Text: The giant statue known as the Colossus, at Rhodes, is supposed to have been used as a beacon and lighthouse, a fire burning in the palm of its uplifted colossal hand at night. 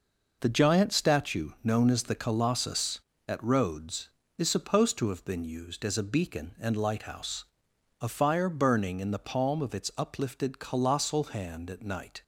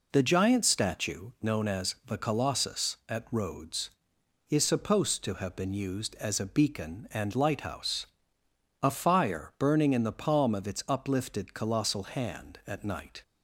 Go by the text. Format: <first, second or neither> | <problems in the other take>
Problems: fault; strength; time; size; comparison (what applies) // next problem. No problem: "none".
neither | none